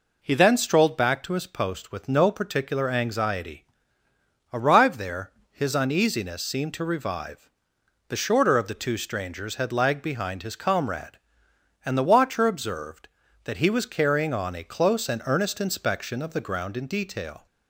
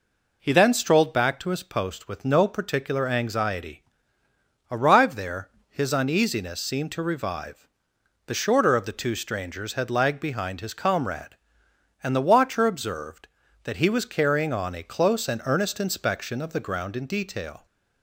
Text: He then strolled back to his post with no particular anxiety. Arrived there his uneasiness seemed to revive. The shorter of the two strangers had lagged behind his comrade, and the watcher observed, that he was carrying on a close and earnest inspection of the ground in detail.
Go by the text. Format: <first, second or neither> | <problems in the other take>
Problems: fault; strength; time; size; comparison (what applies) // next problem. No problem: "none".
neither | pauses between "there" and "his"; slight; the same in both